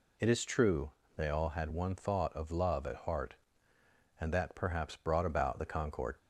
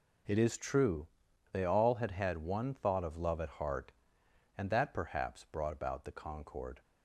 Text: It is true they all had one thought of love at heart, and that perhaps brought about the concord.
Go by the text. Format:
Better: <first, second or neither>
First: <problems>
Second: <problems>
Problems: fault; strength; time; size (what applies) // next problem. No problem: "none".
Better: first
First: pauses between "true" and "they"; slight; at 0.9 s; 0.24 s long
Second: pauses between "true" and "they"; at 1.0 s; 0.44 s long // says "had" twice; at 2.1 s